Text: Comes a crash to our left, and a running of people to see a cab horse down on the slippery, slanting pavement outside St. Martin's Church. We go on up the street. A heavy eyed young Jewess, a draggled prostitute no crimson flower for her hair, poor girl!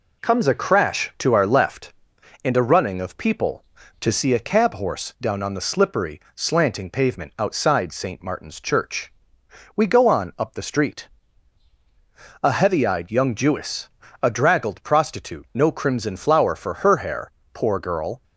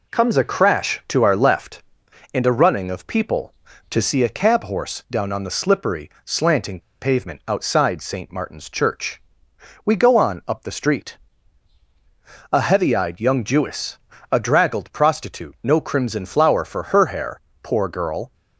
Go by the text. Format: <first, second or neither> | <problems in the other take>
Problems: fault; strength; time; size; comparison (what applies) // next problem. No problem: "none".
first | pauses between "slanting" and "pavement"; slight; at 6.8 s; 0.20 s long